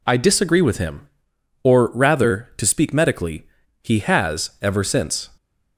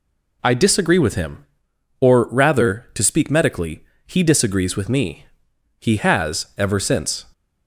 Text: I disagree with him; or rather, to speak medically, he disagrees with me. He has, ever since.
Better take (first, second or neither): second